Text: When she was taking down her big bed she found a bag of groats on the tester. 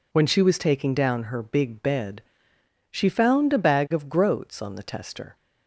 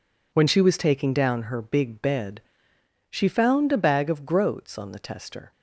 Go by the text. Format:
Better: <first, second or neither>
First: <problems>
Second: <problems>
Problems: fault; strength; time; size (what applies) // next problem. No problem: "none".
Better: first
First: pauses between "bed" and "she"; noticeable; at 2.2 s; 0.72 s long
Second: gets quieter; strong; throughout; 10.5 dB // pauses between "bed" and "she"; noticeable; at 2.4 s; 0.72 s long